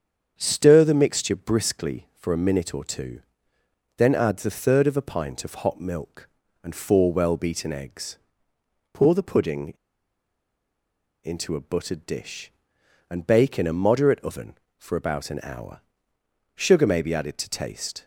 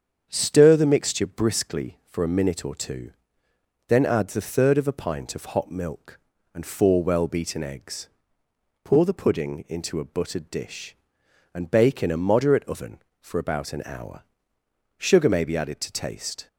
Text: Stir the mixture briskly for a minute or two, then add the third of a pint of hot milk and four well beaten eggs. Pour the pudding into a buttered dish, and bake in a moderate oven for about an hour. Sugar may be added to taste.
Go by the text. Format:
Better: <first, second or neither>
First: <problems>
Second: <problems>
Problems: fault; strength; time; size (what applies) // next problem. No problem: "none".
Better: second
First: starts louder than the rest; strong; until 1.3 s; 7.5 dB // pauses between "pudding" and "into"; strong; at 9.7 s; 1.5 s long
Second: starts louder than the rest; strong; until 1.3 s; 7.5 dB